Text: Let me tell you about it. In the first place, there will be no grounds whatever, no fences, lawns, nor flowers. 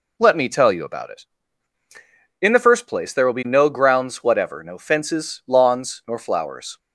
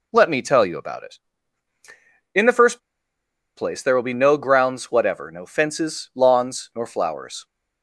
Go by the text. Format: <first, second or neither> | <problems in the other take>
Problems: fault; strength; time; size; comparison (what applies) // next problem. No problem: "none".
first | pauses between "first" and "place"; noticeable; at 2.7 s; 0.76 s long